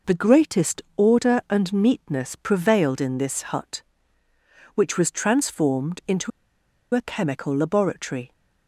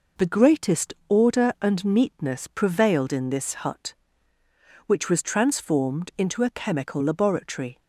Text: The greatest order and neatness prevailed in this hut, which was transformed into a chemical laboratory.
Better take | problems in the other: second | pauses between "into" and "a"; noticeable; at 6.3 s; 0.64 s long

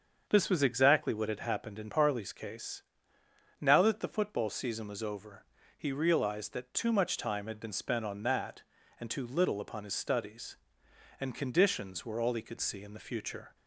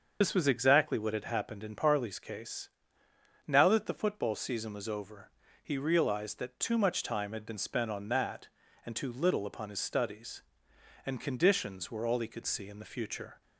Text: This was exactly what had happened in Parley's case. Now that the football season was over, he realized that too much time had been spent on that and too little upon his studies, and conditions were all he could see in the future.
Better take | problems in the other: first | loses the start of "This"; at 0.2 s; 70 ms // starts louder than the rest; until 1.2 s; 6.5 dB; also in the first

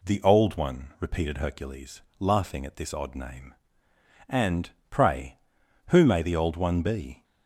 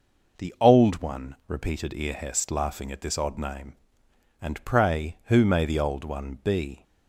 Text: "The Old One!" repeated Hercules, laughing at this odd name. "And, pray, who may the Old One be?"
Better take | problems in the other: first | says "Earhest" for "Hercules"; at 1.9 s

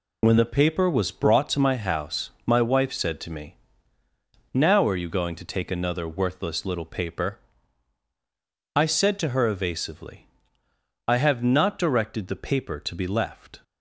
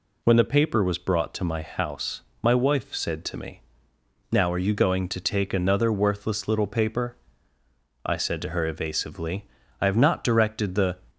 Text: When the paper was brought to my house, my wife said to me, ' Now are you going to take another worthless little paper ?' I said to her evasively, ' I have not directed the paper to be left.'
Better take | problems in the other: first | stops before "paper to be left"; at 11.0 s

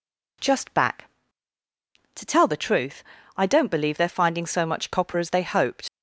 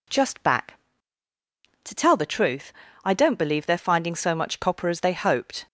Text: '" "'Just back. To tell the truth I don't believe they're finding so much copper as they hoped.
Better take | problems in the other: second | pauses between "truth" and "I"; slight; at 3.0 s; 0.32 s long; slight in the second // leaves "hoped" unfinished; at 5.8 s; 85 ms

